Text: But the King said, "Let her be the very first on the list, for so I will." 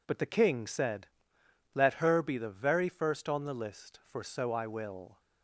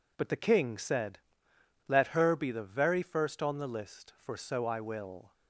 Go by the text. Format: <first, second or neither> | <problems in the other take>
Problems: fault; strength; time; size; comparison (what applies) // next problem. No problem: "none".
neither | none